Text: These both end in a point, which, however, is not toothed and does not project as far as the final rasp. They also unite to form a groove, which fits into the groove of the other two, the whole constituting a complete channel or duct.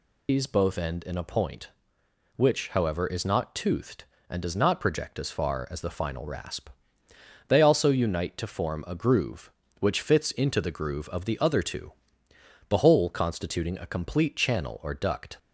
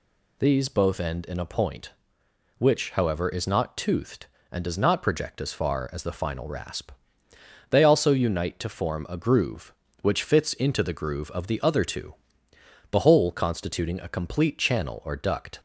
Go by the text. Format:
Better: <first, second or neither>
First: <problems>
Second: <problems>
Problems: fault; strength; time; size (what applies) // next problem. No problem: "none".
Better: second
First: loses the start of "These"; at 0.2 s; 110 ms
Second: none